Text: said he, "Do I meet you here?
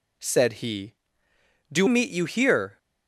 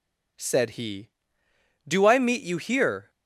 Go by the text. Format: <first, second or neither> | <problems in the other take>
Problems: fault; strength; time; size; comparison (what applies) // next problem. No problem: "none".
second | skips "I"; at 1.8 s